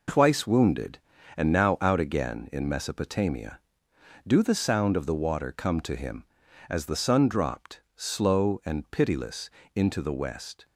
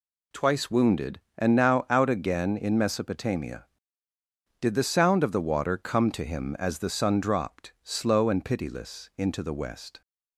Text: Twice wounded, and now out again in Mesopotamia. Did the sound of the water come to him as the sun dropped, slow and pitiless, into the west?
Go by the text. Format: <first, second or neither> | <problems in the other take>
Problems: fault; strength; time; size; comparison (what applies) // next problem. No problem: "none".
second | says "Do" for "Did"; at 4.2 s